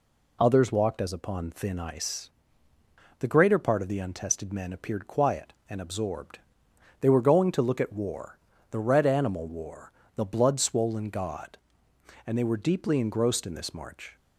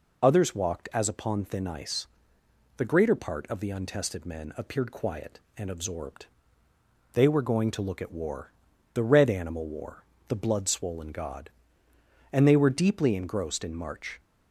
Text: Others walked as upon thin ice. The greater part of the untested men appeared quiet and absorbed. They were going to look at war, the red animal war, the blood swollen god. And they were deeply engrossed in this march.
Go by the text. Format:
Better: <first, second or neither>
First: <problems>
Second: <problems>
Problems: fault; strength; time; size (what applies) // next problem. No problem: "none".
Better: first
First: none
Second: skips "this"; at 13.7 s